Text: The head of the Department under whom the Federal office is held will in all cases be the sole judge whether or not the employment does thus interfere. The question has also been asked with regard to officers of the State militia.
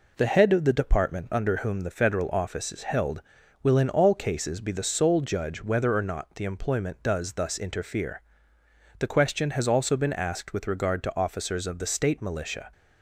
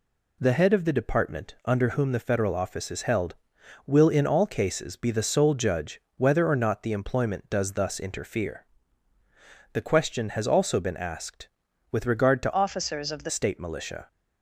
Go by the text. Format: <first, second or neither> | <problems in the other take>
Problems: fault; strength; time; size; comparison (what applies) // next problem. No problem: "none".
first | pauses between "judge" and "whether"; slight; at 6.0 s; 0.16 s long // changes voice from "officers" to "the"; from 12.5 to 13.3 s; 0.8 s long